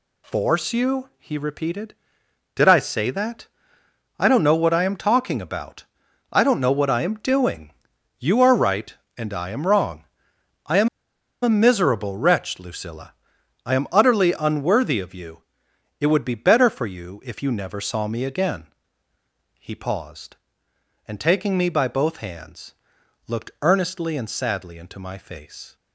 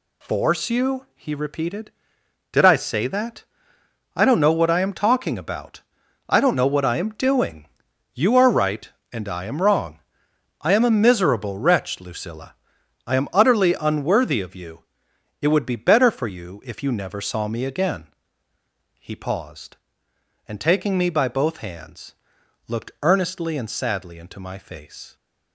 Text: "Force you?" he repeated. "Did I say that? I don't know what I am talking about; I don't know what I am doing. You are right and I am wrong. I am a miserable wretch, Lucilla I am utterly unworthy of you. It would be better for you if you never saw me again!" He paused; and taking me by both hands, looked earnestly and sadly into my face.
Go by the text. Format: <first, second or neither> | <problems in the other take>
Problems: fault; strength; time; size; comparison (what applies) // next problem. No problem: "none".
second | pauses between "am" and "a"; noticeable; at 10.8 s; 0.54 s long // pauses between "Lucilla" and "I"; noticeable; at 13.1 s; 0.52 s long; noticeable in the second